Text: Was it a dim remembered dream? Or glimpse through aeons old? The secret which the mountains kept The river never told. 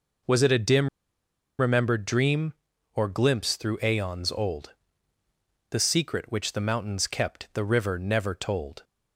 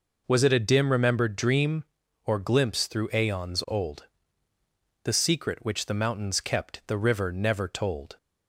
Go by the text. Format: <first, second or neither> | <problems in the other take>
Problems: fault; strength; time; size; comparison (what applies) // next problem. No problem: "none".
second | pauses between "dim" and "remembered"; noticeable; at 0.8 s; 0.70 s long